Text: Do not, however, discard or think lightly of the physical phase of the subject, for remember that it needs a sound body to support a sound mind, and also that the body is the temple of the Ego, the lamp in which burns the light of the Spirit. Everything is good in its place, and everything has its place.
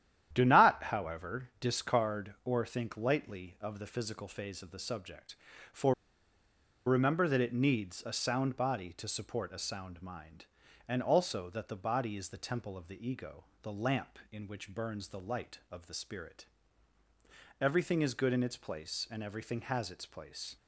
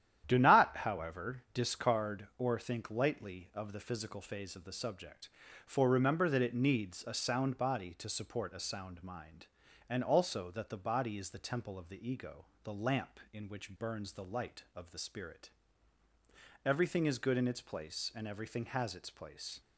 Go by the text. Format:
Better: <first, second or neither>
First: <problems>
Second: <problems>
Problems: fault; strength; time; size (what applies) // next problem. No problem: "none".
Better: second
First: starts louder than the rest; strong; until 1.3 s; 10.5 dB // pauses between "for" and "remember"; noticeable; at 5.9 s; 0.92 s long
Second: starts louder than the rest; strong; until 1.2 s; 10.5 dB